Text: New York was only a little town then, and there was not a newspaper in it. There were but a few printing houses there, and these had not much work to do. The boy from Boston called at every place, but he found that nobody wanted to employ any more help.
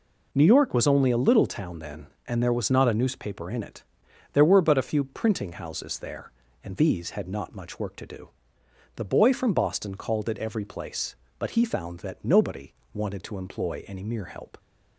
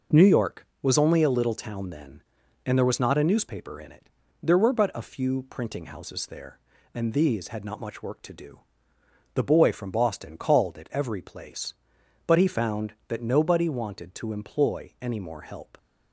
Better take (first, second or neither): second